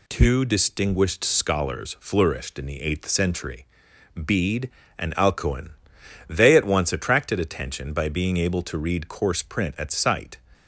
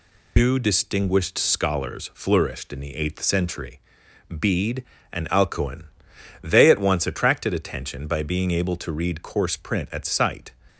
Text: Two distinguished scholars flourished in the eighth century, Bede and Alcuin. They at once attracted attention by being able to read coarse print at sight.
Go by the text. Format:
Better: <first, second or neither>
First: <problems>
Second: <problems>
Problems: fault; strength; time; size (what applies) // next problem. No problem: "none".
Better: first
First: none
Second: loses the start of "Two"; at 0.3 s; 140 ms